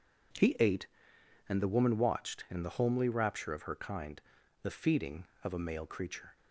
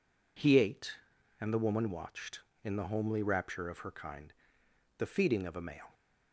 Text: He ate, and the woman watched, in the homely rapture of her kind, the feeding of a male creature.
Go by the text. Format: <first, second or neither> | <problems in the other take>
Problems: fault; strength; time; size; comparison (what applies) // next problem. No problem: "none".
first | stops before "creature"; at 5.9 s